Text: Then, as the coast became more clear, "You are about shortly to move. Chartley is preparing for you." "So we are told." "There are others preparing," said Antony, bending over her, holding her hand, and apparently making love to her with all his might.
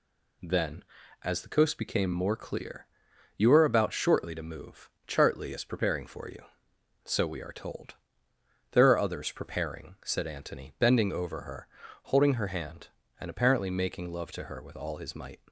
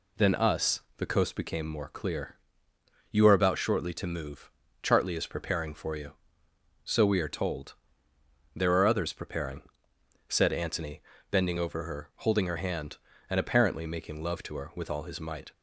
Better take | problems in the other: first | says "us" for "as"; at 0.3 s

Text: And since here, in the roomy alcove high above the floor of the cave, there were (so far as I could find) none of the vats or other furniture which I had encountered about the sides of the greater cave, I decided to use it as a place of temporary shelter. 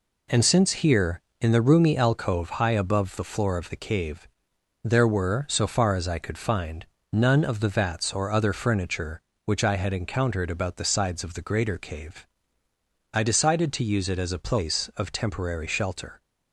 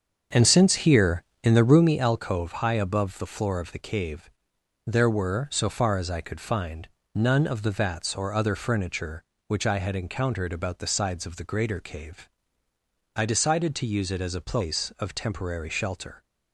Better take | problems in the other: first | starts louder than the rest; strong; until 1.9 s; 7 dB

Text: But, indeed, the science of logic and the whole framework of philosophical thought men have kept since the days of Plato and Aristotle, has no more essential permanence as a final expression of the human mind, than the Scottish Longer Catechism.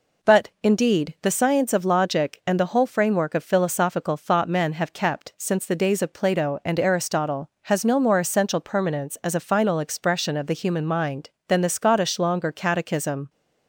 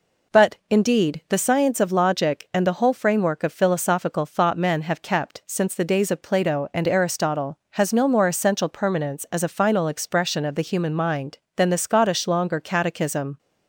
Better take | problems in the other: neither | none

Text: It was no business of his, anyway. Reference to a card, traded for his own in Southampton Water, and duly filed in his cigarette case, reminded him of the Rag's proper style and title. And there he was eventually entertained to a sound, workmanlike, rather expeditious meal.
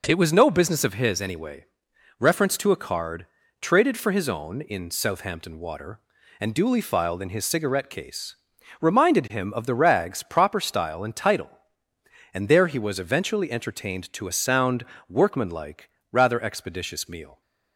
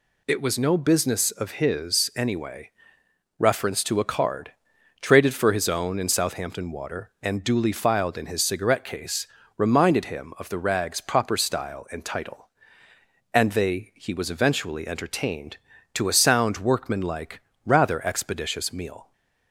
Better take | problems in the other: first | says "they" for "there"; at 13.5 s

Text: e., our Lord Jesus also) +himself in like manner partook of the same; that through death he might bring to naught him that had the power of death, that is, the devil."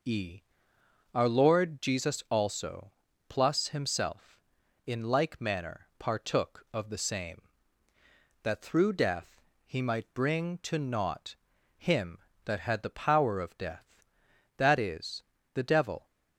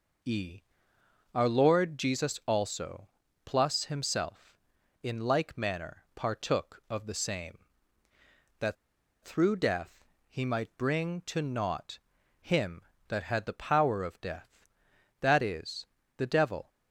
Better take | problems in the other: first | pauses between "that" and "through"; noticeable; at 8.7 s; 0.49 s long // pauses between "death" and "he"; slight; at 10.0 s; 0.24 s long; slight in the first // pauses between "naught" and "him"; at 11.9 s; 0.42 s long; also in the first

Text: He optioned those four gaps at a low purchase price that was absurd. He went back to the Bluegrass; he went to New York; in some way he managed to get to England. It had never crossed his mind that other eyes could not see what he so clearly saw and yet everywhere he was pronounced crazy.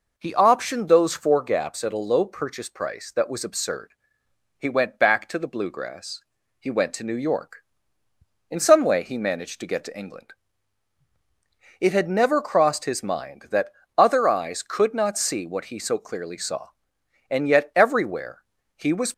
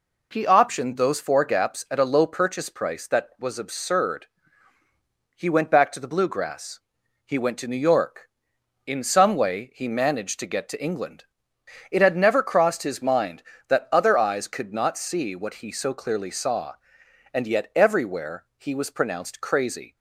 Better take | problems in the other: second | pauses between "that" and "other"; slight; at 13.7 s; 0.26 s long // pauses between "everywhere" and "he"; slight; at 18.4 s; 0.34 s long // stops before "pronounced crazy"; at 19.1 s

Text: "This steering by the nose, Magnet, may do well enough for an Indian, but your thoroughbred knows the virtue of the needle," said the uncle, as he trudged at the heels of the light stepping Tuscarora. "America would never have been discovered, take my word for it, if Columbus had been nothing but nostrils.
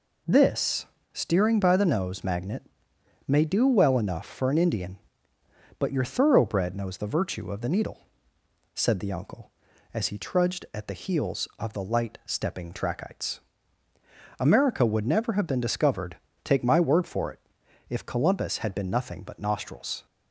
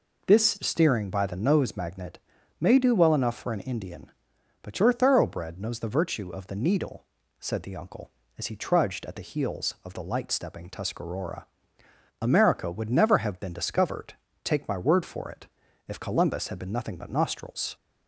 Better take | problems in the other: second | pauses between "This" and "steering"; slight; at 0.8 s; 0.26 s long // says "Trachytes" for "Tuscarora"; at 12.7 s

